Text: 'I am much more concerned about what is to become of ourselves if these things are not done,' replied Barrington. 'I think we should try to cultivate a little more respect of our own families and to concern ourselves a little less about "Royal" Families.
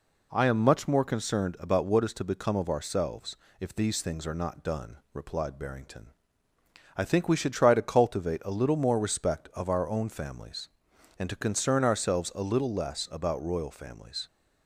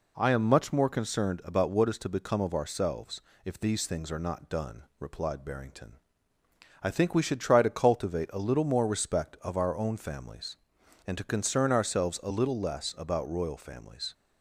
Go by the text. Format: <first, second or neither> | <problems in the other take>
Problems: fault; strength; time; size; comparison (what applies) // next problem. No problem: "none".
neither | pauses between "ourselves" and "if"; slight; the same in both